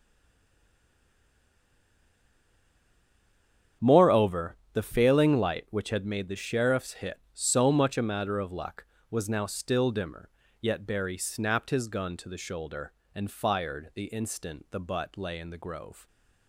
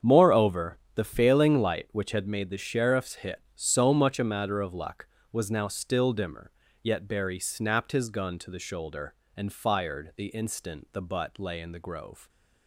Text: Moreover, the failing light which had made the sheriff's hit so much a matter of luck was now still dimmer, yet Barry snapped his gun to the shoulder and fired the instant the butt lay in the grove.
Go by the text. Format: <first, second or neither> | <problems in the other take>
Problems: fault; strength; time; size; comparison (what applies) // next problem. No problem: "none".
second | stays silent before the first word; strong; until 3.8 s; 3.8 s long // starts louder than the rest; strong; until 4.9 s; 7.5 dB; strong in the second